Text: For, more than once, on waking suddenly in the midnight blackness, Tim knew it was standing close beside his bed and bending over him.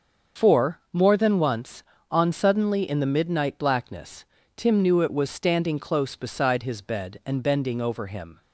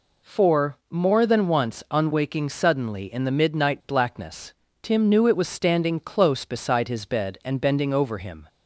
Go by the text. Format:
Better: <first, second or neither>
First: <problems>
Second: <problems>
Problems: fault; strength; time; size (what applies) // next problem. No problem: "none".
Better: second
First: starts louder than the rest; until 1.5 s; 6.5 dB // skips "waking"; at 2.3 s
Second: none